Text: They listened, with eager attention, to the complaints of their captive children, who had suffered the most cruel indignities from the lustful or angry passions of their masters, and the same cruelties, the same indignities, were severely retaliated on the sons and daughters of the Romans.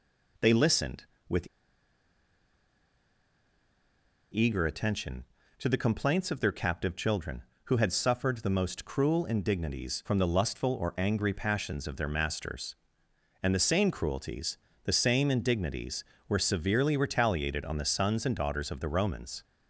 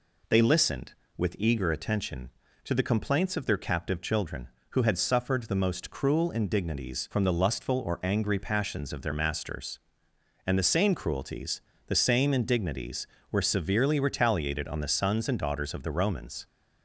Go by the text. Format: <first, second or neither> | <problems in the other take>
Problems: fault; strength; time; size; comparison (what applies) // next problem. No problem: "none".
second | pauses between "with" and "eager"; strong; at 1.4 s; 2.8 s long